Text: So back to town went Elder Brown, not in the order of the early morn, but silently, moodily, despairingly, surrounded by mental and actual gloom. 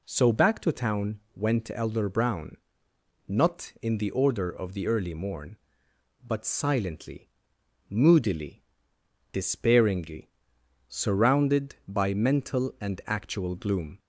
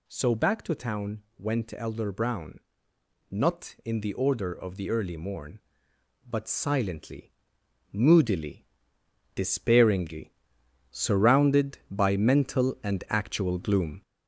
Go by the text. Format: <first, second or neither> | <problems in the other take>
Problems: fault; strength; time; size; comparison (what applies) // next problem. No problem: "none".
first | gets louder; noticeable; throughout; 4.5 dB